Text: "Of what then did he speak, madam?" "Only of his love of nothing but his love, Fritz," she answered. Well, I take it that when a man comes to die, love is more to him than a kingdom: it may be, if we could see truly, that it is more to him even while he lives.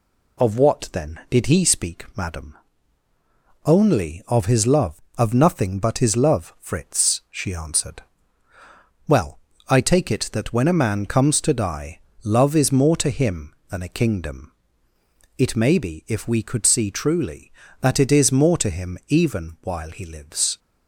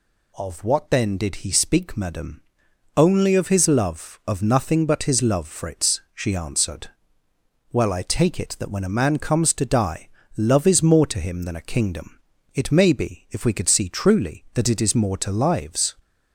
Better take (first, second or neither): first